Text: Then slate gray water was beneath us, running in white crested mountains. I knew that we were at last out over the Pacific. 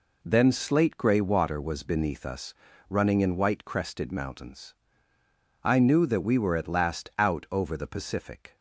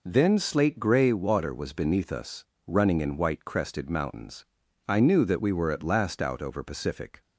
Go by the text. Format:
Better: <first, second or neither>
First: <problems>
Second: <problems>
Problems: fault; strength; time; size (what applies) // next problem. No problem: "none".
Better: first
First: none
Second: skips "the"; at 6.6 s